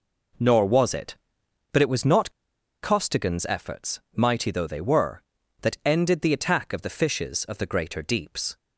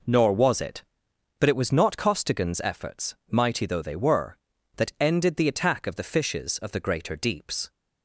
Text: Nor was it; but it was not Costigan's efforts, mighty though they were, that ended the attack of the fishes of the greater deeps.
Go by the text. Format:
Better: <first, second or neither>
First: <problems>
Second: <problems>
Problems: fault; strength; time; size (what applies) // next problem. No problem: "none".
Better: second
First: pauses between "not" and "Costigan's"; noticeable; at 2.3 s; 0.52 s long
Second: none